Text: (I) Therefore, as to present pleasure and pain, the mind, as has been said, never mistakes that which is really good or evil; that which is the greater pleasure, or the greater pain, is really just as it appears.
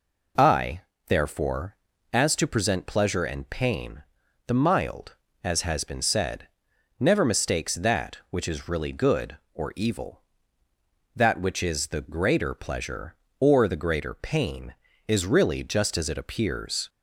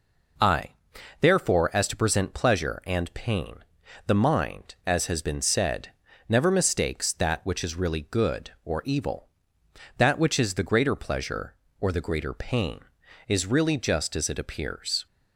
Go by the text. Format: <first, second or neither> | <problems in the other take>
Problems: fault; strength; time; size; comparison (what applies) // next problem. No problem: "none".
second | says "mild" for "mind"; at 4.5 s